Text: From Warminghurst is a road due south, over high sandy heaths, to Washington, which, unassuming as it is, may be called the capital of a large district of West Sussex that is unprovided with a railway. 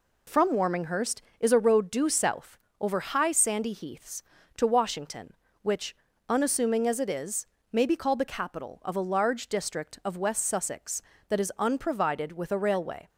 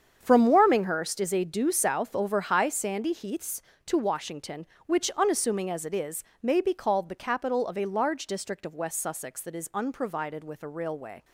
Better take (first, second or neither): first